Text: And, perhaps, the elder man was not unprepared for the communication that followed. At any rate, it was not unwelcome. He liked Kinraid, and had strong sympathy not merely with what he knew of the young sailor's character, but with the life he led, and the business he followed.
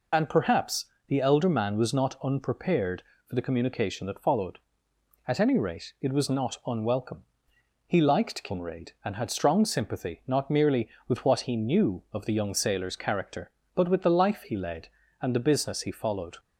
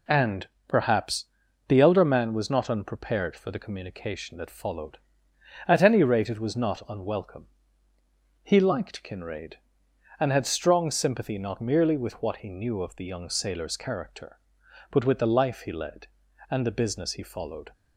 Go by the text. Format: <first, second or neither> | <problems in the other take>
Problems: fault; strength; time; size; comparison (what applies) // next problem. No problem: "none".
second | loses the start of "And"; at 0.1 s; 35 ms